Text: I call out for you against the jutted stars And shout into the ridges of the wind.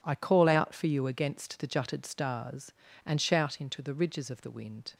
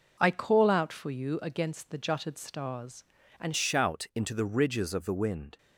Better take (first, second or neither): first